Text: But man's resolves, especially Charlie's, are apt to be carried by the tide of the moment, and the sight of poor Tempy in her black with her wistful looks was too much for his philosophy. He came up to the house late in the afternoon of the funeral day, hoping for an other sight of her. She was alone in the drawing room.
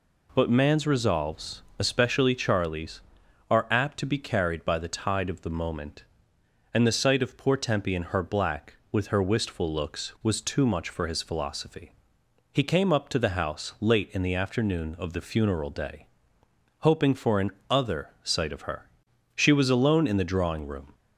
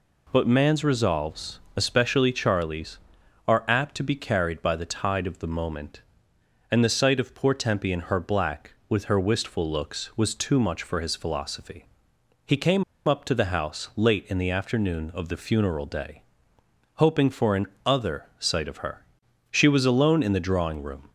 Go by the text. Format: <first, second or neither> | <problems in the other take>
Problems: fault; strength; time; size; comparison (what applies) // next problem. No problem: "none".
first | pauses between "came" and "up"; slight; at 12.8 s; 0.24 s long // pauses between "an" and "other"; slight; at 17.6 s; 0.18 s long; slight in the first